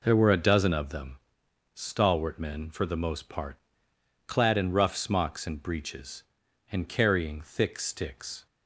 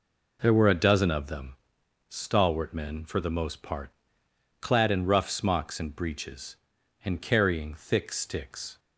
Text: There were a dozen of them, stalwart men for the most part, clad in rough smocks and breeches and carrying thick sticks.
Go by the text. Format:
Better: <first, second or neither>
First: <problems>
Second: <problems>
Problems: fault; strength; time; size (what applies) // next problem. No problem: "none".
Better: neither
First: none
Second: none